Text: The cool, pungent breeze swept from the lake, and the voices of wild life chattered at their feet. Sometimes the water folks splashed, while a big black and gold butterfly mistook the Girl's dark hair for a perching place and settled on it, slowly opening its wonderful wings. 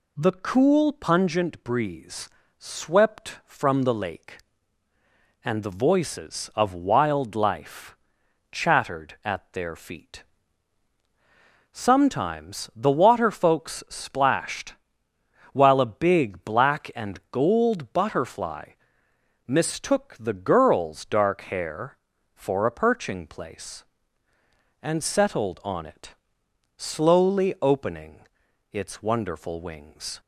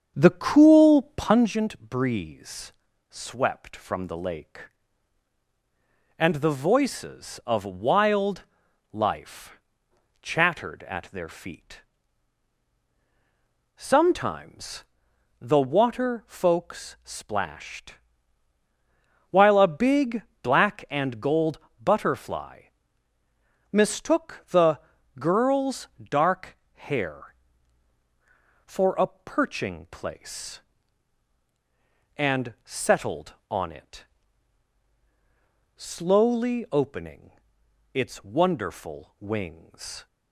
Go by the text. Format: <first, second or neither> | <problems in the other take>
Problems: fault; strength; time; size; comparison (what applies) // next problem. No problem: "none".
first | starts louder than the rest; strong; until 1.5 s; 7.5 dB // pauses between "breeze" and "swept"; slight; at 2.7 s; 0.34 s long; slight in the first // pauses between "wild" and "life"; noticeable; at 8.4 s; 0.48 s long // pauses between "life" and "chattered"; noticeable; at 9.5 s; 0.66 s long; noticeable in the first // pauses between "Sometimes" and "the"; noticeable; at 14.8 s; 0.56 s long // pauses between "big" and "black"; slight; at 20.2 s; 0.18 s long // pauses between "gold" and "butterfly"; slight; at 21.6 s; 0.22 s long // pauses between "butterfly" and "mistook"; at 22.6 s; 1.0 s long; noticeable in the first // pauses between "the" and "Girl's"; at 24.7 s; 0.40 s long // pauses between "dark" and "hair"; slight; at 26.5 s; 0.18 s long // pauses between "opening" and "its"; noticeable; at 37.3 s; 0.60 s long; noticeable in the first